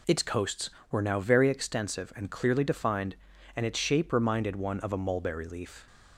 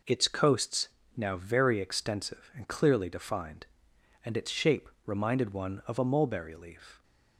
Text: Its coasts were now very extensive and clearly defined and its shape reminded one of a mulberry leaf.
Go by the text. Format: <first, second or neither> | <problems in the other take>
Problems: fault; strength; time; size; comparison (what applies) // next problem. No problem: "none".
first | skips "were"; at 1.0 s // pauses between "shape" and "reminded"; slight; at 4.8 s; 0.16 s long